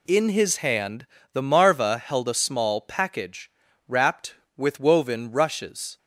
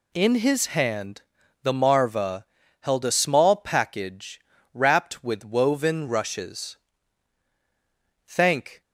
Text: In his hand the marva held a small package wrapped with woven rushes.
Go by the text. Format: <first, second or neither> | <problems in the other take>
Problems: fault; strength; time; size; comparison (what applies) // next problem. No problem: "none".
first | pauses between "hand" and "the"; at 1.2 s; 0.40 s long; slight in the first // pauses between "marva" and "held"; slight; at 2.4 s; 0.36 s long // pauses between "package" and "wrapped"; slight; at 4.4 s; 0.32 s long; also in the first // goes on to say "Thank"; from 8.2 s on; 0.56 s long